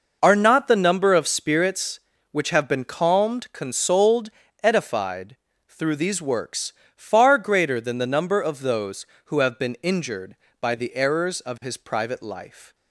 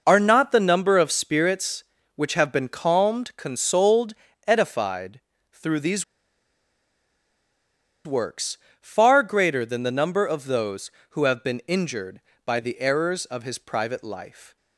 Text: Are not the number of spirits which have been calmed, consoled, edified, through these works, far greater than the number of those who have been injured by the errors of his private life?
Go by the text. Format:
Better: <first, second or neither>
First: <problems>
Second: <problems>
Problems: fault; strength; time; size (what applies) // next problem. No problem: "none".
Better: first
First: none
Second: pauses between "these" and "works"; strong; at 6.0 s; 2.0 s long